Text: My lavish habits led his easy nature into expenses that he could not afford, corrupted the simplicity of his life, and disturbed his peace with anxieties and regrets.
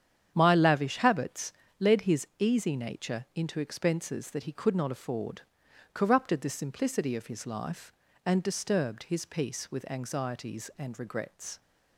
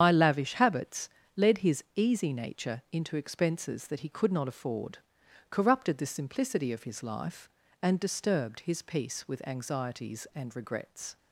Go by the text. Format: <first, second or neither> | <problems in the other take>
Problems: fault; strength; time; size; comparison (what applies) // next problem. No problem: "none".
first | loses the start of "My"; at 0.0 s; 85 ms // starts louder than the rest; strong; until 1.0 s; 8.5 dB; strong in the first // pauses between "habits" and "led"; slight; at 1.0 s; 0.26 s long; slight in the first